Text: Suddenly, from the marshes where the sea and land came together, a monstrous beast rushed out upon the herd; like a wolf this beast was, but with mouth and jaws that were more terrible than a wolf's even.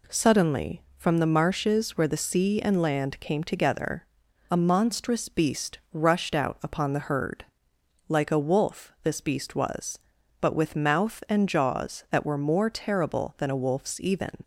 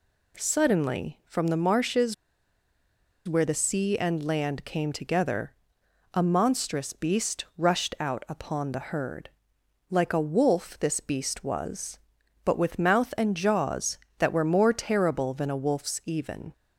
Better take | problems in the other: first | pauses between "marshes" and "where"; at 2.1 s; 1.1 s long

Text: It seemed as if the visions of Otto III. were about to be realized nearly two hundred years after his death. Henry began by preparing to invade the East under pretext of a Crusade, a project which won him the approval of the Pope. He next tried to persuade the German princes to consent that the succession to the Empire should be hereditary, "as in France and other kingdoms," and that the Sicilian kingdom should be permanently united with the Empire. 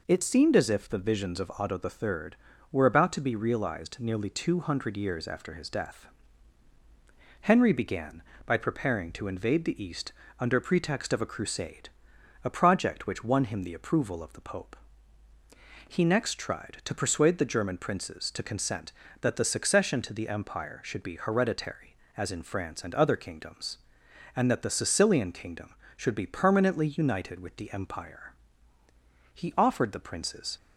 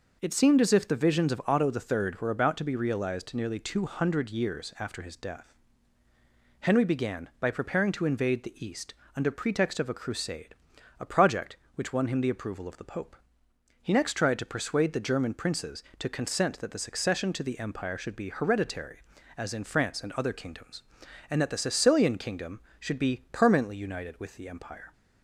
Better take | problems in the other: second | pauses between "East" and "under"; slight; at 10.1 s; 0.28 s long; slight in the second // goes on to say "He offered the princes"; noticeable; from 29.3 s on; 1.2 s long

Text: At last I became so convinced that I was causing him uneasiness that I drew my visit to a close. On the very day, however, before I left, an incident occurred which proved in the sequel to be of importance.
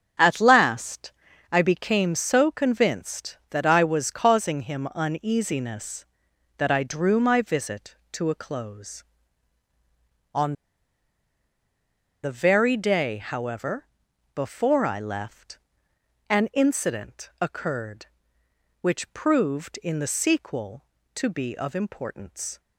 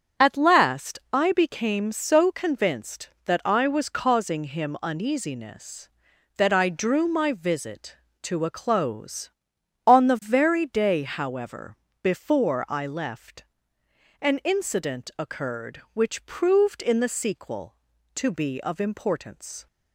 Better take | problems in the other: second | starts louder than the rest; strong; until 1.6 s; 7.5 dB; strong in the second // pauses between "last" and "I"; at 1.1 s; 0.40 s long // pauses between "On" and "the"; strong; at 10.5 s; 1.7 s long

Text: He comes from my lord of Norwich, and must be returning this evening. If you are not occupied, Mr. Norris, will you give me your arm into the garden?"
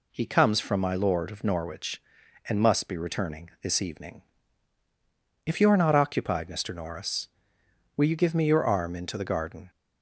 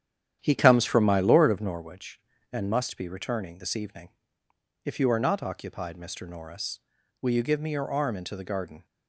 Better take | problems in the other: first | starts louder than the rest; strong; until 1.9 s; 10 dB

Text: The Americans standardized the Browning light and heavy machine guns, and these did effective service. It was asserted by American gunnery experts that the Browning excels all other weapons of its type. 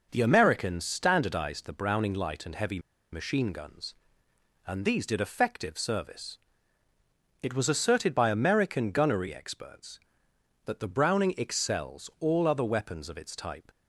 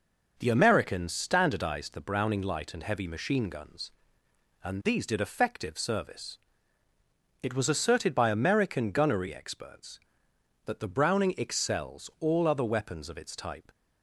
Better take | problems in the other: second | pauses between "heavy" and "machine"; slight; at 2.7 s; 0.34 s long

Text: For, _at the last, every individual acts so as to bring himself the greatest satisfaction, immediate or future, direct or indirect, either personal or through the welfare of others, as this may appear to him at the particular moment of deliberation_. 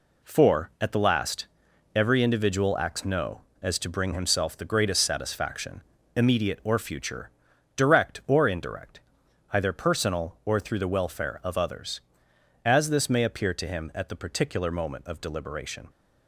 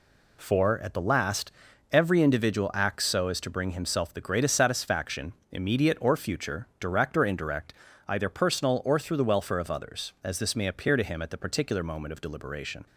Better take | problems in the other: second | says "no" for "so"; at 3.0 s

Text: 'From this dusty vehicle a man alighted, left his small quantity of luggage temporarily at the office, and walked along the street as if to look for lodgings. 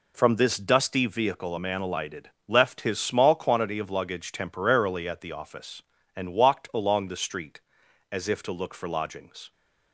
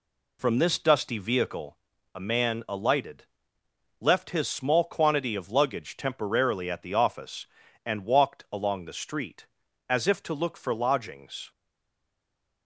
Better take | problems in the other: first | pauses between "vehicle" and "a"; at 1.7 s; 0.38 s long // stays silent after the last word; from 11.5 s on; 1.1 s long

